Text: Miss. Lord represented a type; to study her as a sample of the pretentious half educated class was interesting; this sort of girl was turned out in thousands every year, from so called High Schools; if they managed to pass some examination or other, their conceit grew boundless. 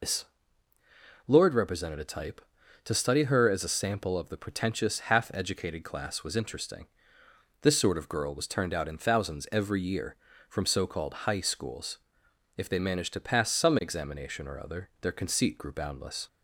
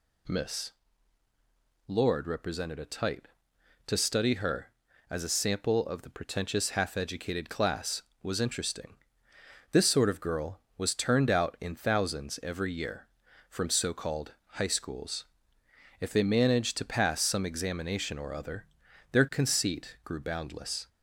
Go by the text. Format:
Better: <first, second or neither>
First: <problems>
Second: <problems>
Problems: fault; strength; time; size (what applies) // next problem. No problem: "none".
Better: second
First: loses the start of "Miss"; at 0.0 s; 135 ms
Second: none